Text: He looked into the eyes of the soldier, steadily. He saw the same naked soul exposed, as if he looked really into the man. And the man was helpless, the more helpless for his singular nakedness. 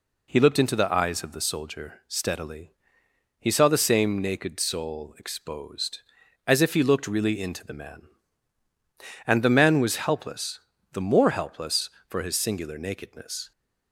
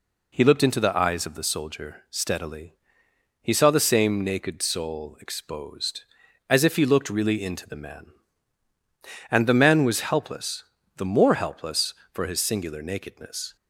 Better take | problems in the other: neither | none

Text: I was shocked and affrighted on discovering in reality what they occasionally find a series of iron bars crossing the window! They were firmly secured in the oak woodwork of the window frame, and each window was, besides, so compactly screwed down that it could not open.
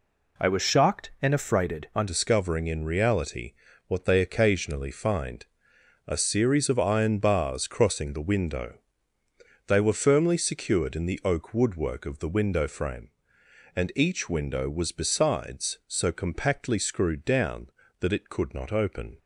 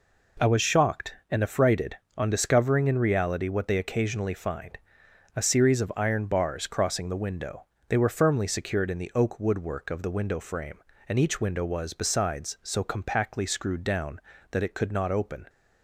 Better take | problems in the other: second | changes voice at "discovering"; from 2.0 s on; 17.1 s long // pauses between "reality" and "what"; slight; at 3.5 s; 0.36 s long // pauses between "find" and "a"; noticeable; at 5.4 s; 0.62 s long; noticeable in the second

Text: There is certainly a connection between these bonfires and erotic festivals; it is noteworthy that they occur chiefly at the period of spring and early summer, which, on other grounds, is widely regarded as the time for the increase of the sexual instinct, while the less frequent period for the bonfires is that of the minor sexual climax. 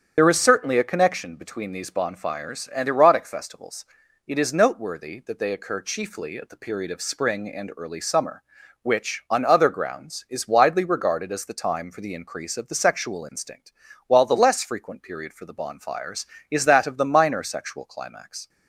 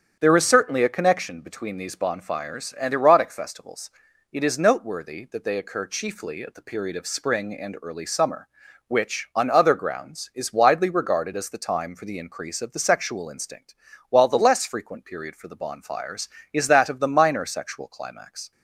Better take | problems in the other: second | loses the start of "There"; at 0.1 s; 50 ms // starts louder than the rest; strong; until 1.1 s; 8.5 dB; strong in the second

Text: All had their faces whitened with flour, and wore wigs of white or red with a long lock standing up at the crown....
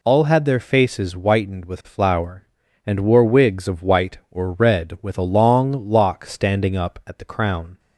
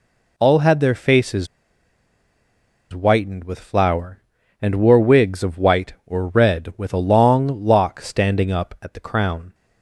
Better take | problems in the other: first | pauses between "faces" and "whitened"; strong; at 1.4 s; 1.4 s long

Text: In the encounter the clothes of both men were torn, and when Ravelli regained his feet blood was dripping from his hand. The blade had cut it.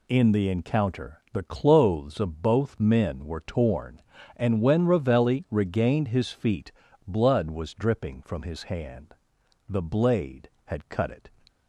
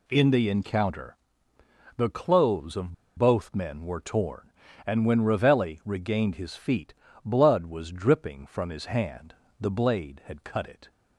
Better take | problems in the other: first | pauses between "encounter" and "the"; noticeable; at 1.1 s; 0.80 s long // pauses between "of" and "both"; slight; at 2.9 s; 0.22 s long // pauses between "feet" and "blood"; slight; at 6.9 s; 0.32 s long; slight in the first

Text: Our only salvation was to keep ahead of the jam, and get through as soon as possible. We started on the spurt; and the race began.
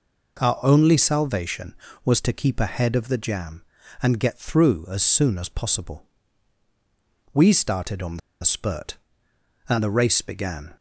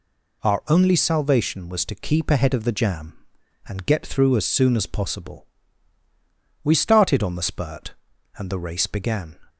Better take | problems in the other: second | pauses between "on" and "the"; slight; at 8.1 s; 0.23 s long

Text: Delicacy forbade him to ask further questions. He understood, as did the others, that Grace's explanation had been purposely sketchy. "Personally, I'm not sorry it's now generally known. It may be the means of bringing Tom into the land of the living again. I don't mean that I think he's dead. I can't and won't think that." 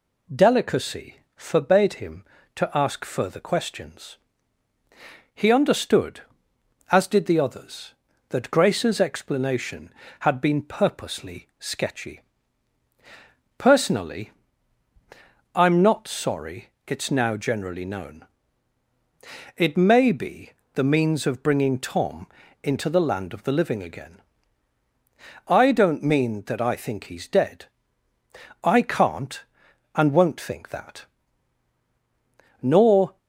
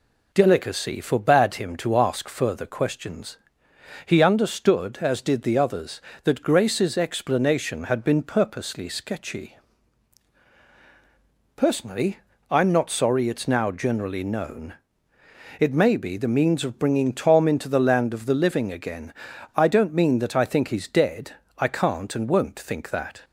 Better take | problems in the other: second | pauses between "Delicacy" and "forbade"; slight; at 1.1 s; 0.18 s long // pauses between "sorry" and "it's"; slight; at 16.6 s; 0.20 s long // pauses between "be" and "the"; slight; at 20.5 s; 0.22 s long // pauses between "Tom" and "into"; slight; at 22.2 s; 0.34 s long // goes on to say "Nor"; from 32.6 s on; 0.56 s long

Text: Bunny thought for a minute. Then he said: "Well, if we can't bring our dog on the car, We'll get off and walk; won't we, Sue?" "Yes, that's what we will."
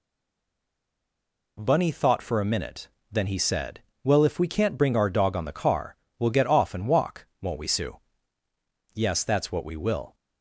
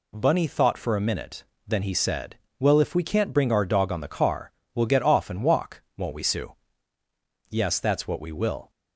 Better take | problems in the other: second | stays silent before the first word; noticeable; until 1.5 s; 1.5 s long

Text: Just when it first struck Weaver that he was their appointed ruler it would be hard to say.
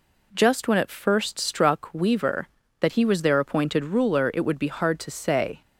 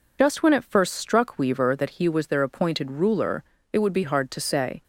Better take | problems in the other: first | loses the start of "Just"; at 0.1 s; 40 ms // pauses between "ruler" and "it"; slight; at 3.4 s; 0.28 s long

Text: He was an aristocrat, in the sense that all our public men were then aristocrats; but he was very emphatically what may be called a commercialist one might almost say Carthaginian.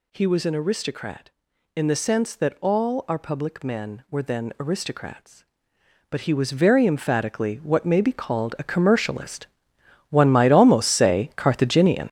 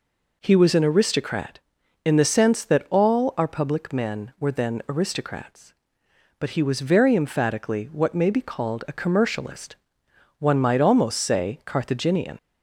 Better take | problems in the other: second | gets louder; strong; throughout; 9 dB // pauses between "commercialist" and "one"; noticeable; at 9.4 s; 0.64 s long; noticeable in the second

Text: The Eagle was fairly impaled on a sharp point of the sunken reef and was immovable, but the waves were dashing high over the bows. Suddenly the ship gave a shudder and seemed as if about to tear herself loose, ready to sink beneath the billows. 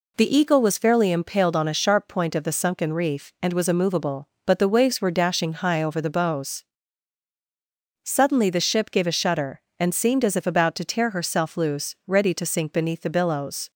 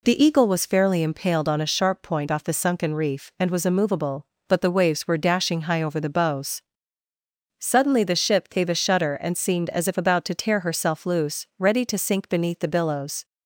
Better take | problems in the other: first | says "off" for "of"; at 2.3 s

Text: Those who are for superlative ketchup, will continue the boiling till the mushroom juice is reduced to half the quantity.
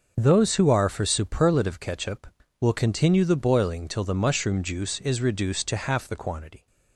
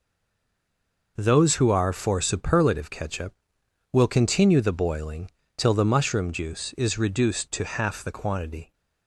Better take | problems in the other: first | stays silent before the first word; until 1.1 s; 1.1 s long // pauses between "boiling" and "till"; slight; at 5.2 s; 0.26 s long

